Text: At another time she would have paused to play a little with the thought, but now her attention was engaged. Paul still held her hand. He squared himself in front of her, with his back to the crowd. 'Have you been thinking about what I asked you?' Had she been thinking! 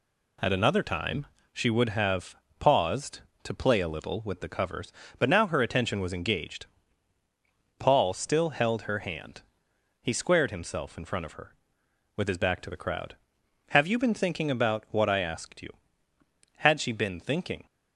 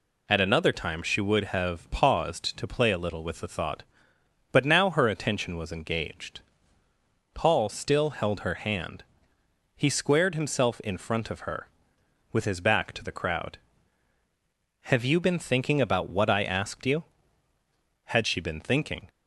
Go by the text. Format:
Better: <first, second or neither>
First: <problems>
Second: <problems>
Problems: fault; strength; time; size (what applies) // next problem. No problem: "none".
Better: second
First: pauses between "time" and "she"; slight; at 1.2 s; 0.26 s long // pauses between "have" and "paused"; slight; at 2.3 s; 0.24 s long // says "covers" for "thought"; at 4.4 s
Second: none